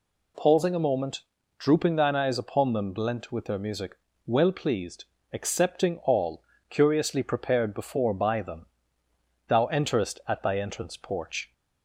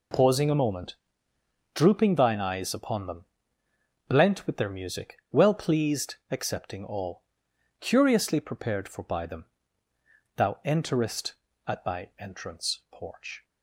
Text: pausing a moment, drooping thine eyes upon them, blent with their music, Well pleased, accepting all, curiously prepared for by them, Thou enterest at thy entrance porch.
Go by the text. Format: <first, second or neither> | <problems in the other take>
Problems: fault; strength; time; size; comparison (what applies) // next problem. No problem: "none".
second | says "before" for "for"; at 7.7 s